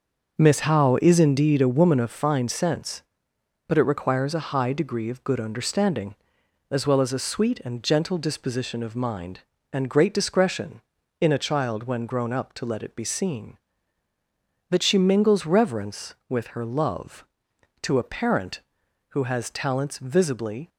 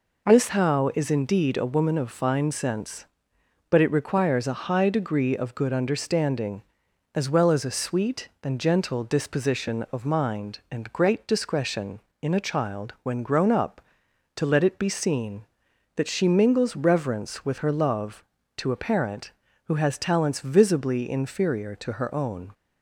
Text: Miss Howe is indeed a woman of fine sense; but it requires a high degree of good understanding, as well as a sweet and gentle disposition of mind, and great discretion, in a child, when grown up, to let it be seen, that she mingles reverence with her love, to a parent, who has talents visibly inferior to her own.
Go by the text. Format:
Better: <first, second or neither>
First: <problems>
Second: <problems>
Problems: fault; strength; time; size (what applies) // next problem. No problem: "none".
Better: second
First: stops before "inferior to her own"; at 20.6 s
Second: none